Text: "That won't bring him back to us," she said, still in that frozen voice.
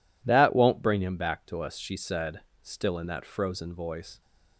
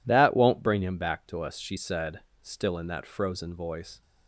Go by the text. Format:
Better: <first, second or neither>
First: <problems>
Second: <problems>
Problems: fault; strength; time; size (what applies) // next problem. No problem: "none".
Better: neither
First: none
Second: none